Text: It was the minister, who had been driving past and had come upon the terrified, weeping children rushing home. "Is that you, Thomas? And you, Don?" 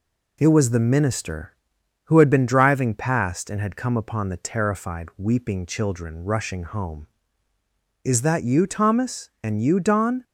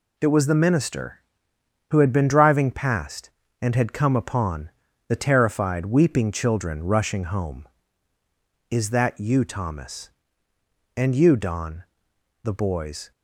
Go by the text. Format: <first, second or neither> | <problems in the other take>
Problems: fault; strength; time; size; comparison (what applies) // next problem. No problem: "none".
first | pauses between "upon" and "the"; at 4.7 s; 0.38 s long // goes on to say "The boys"; noticeable; from 12.4 s on; 0.68 s long